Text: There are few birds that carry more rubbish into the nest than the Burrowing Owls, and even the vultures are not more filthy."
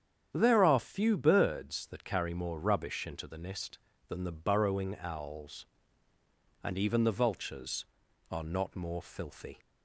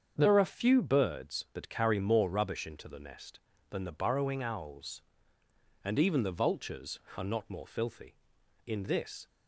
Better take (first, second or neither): first